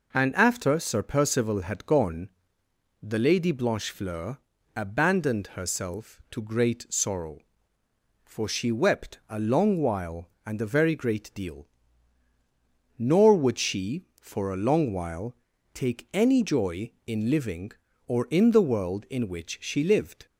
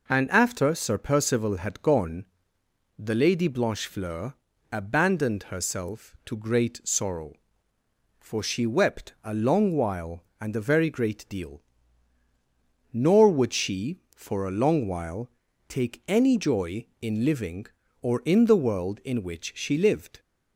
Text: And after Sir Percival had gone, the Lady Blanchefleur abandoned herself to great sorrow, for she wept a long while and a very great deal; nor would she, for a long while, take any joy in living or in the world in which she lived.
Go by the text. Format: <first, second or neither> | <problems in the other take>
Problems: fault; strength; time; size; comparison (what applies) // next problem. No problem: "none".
neither | pauses between "Blanchefleur" and "abandoned"; the same in both